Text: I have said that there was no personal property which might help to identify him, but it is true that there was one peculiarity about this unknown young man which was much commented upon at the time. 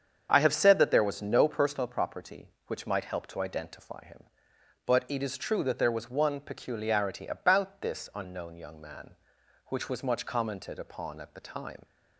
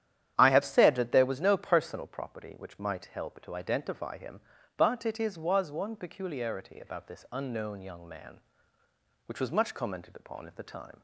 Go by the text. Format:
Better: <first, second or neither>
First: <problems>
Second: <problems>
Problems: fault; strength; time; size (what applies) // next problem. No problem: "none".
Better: first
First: starts louder than the rest; strong; until 1.3 s; 7.5 dB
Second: starts louder than the rest; strong; until 1.3 s; 10.5 dB // skips "true that there"; at 5.3 s